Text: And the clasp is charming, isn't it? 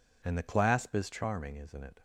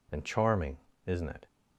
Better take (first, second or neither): first